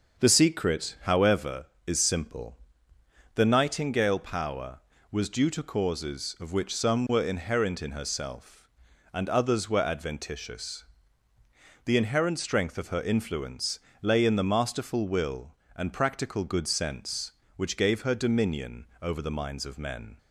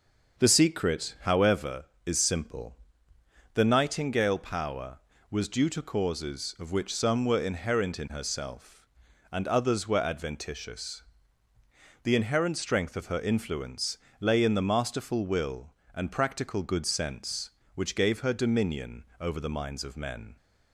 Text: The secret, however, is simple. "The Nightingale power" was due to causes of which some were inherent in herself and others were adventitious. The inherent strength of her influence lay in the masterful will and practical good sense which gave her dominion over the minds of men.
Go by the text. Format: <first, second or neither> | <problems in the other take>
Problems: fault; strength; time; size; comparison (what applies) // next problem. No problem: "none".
neither | starts louder than the rest; the same in both // pauses between "influence" and "lay"; slight; the same in both